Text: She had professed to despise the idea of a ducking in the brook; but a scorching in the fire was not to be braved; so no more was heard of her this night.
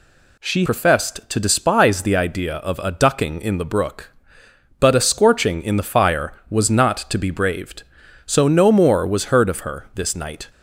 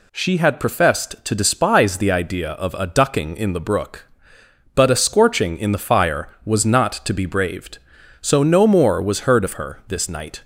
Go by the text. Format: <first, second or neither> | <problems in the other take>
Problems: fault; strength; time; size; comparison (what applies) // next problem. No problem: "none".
second | skips "had"; at 0.6 s